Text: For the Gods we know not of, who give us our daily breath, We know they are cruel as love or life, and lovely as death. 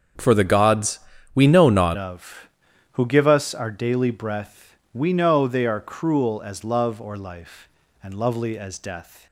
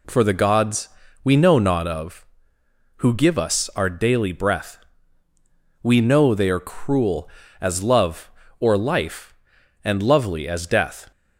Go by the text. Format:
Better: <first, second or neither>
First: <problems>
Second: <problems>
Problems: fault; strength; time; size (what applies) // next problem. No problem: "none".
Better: second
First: starts louder than the rest; strong; until 1.5 s; 7 dB // pauses between "Gods" and "we"; slight; at 0.9 s; 0.36 s long // changes voice at "of"; from 1.9 s on; 7.3 s long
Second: pauses between "Gods" and "we"; slight; at 0.8 s; 0.36 s long